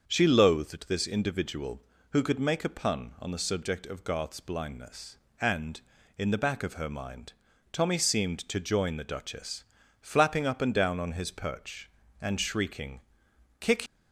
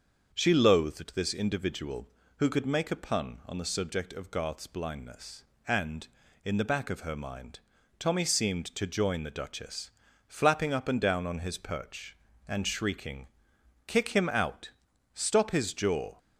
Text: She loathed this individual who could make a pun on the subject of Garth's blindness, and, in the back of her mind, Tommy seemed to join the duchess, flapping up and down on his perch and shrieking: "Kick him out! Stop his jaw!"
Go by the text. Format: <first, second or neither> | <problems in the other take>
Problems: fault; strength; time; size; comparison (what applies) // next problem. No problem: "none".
second | starts louder than the rest; until 1.0 s; 6.5 dB; also in the second // stops before "him out Stop his jaw"; at 13.8 s